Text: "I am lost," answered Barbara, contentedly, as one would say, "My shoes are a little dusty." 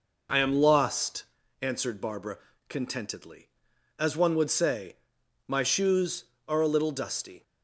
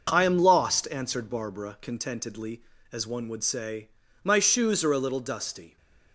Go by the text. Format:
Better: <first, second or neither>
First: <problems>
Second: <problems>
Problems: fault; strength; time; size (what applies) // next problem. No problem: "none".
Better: neither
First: none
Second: none